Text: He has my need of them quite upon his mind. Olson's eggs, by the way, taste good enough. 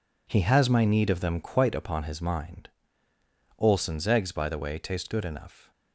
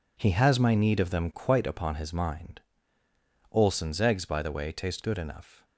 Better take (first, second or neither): neither